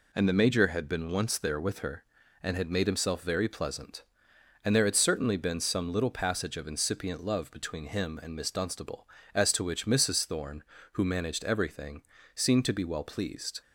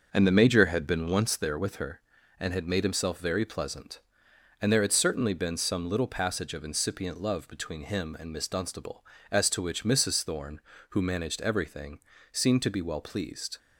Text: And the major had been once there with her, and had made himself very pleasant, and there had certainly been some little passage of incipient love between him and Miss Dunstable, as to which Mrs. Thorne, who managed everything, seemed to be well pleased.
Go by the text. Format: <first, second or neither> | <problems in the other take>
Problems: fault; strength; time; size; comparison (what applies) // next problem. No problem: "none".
first | starts louder than the rest; noticeable; until 1.4 s; 6 dB